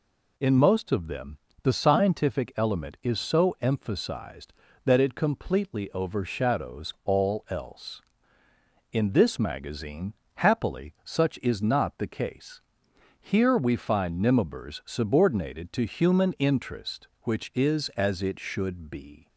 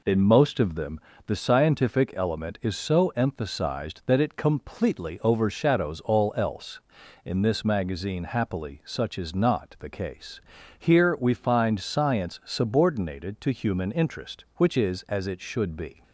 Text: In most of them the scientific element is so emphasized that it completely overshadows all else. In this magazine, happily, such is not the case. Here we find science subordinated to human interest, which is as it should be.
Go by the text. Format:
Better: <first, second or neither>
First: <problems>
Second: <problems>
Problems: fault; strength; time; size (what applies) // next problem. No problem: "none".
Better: second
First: pauses between "them" and "the"; slight; at 1.3 s; 0.26 s long // says "nimibers" for "science"; at 14.2 s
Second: pauses between "them" and "the"; slight; at 0.9 s; 0.28 s long